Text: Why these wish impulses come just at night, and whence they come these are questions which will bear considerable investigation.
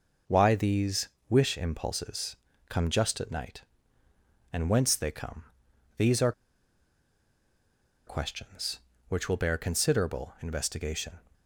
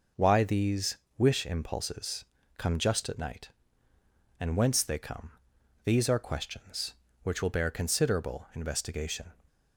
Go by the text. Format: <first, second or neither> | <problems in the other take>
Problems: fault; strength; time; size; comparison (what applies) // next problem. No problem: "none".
second | pauses between "these" and "wish"; slight; at 1.0 s; 0.22 s long; slight in the second // pauses between "impulses" and "come"; slight; at 2.3 s; 0.32 s long; slight in the second // pauses between "come" and "these"; noticeable; at 5.4 s; 0.54 s long; noticeable in the second // pauses between "are" and "questions"; strong; at 6.3 s; 1.7 s long